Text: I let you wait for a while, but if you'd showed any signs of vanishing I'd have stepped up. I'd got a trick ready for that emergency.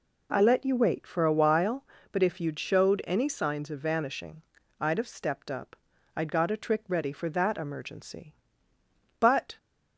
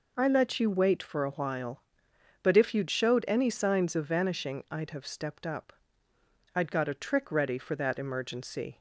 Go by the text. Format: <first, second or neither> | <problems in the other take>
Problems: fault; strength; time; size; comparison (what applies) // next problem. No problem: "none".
second | pauses between "vanishing" and "I'd"; slight; at 4.4 s; 0.36 s long // goes on to say "But"; slight; from 9.1 s on; 0.38 s long